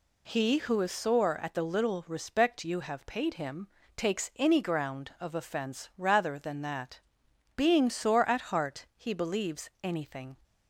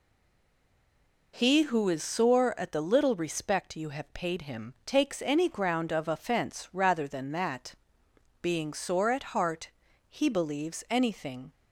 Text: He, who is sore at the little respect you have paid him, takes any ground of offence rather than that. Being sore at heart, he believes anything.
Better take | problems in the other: first | stays silent before the first word; noticeable; until 1.3 s; 1.3 s long

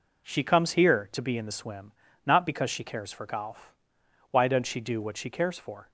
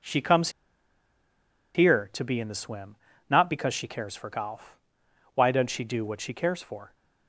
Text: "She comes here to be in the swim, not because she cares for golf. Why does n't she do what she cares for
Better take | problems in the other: first | pauses between "comes" and "here"; strong; at 0.4 s; 1.2 s long

